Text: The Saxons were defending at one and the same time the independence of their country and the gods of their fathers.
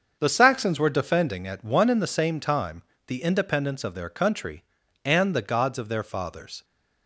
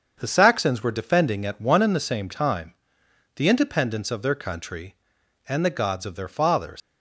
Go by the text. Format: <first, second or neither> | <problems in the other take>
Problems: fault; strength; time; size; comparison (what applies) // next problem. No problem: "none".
first | starts louder than the rest; strong; until 1.1 s; 7 dB; also in the first // pauses between "time" and "the"; noticeable; at 2.7 s; 0.64 s long; slight in the first // leaves "fathers" unfinished; at 6.8 s; 105 ms